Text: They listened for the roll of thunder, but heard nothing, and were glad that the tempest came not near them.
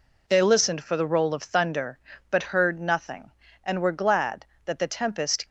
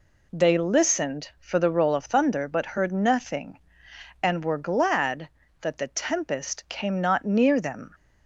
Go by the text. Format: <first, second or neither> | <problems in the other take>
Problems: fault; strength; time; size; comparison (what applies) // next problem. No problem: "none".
second | stops before "came not near them"; at 5.4 s